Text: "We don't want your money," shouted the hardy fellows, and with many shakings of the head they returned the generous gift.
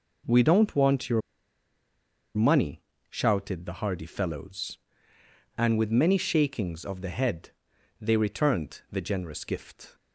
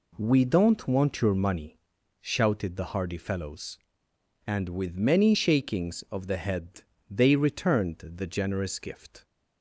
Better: second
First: pauses between "your" and "money"; at 1.2 s; 1.1 s long // pauses between "head" and "they"; noticeable; at 7.5 s; 0.50 s long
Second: pauses between "head" and "they"; slight; at 6.8 s; 0.26 s long

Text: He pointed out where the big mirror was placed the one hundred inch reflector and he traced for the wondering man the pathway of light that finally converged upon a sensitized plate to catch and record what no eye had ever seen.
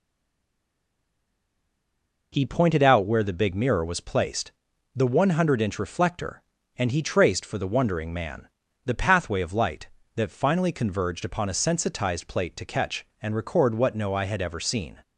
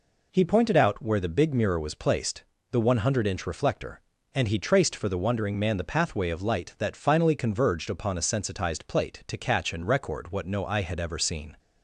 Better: second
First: stays silent before the first word; until 2.3 s; 2.3 s long // pauses between "placed" and "the"; at 4.5 s; 0.44 s long // pauses between "man" and "the"; at 8.4 s; 0.38 s long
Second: pauses between "placed" and "the"; slight; at 2.4 s; 0.28 s long

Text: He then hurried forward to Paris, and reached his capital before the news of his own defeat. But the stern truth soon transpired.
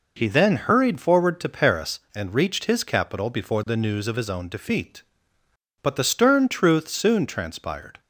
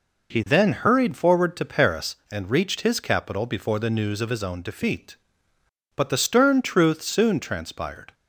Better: neither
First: none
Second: none

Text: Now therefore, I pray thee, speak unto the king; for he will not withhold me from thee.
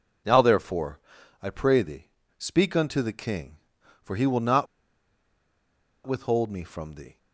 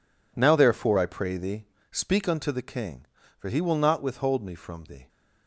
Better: second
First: pauses between "not" and "withhold"; strong; at 4.6 s; 1.4 s long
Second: none

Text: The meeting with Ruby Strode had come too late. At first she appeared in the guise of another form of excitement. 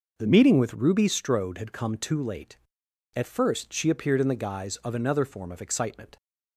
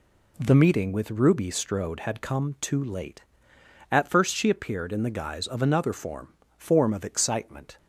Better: first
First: none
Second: says "form" twice; at 6.5 s

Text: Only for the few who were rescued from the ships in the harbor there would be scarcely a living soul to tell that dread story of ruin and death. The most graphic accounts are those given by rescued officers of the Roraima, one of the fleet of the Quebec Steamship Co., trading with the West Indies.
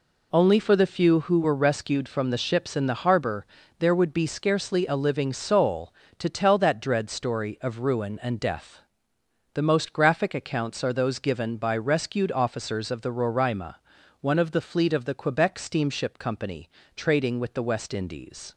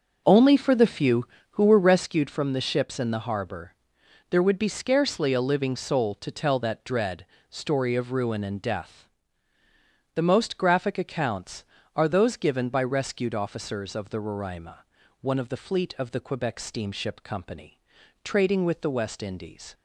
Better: first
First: pauses between "harbor" and "there"; slight; at 3.4 s; 0.36 s long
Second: starts louder than the rest; noticeable; until 2.1 s; 6 dB // pauses between "harbor" and "there"; noticeable; at 3.7 s; 0.56 s long // pauses between "dread" and "story"; slight; at 7.2 s; 0.24 s long

